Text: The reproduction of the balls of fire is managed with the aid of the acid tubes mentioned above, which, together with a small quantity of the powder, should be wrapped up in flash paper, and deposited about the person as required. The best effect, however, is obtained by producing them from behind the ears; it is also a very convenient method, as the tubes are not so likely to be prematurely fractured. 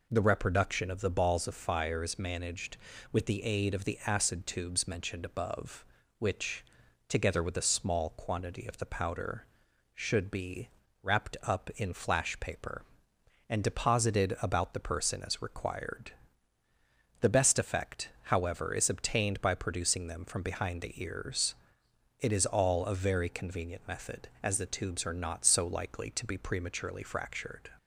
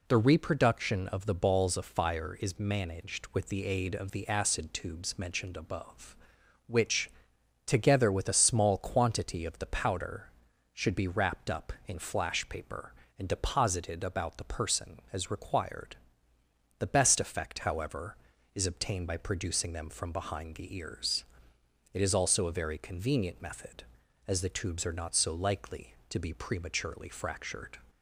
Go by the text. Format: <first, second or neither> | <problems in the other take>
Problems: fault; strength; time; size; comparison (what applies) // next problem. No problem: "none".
second | pauses between "be" and "wrapped"; slight; at 10.6 s; 0.34 s long // says "all" for "also"; at 22.4 s